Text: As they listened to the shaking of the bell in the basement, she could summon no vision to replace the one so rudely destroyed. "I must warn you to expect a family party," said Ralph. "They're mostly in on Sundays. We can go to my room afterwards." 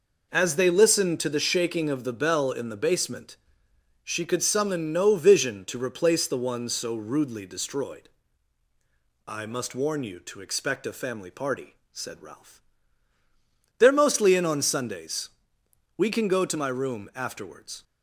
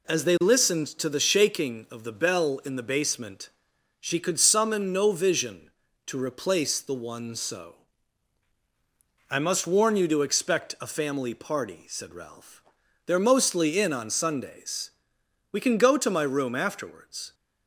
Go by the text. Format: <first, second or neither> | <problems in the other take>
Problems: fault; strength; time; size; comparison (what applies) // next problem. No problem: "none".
first | skips "rudely destroyed"; at 8.5 s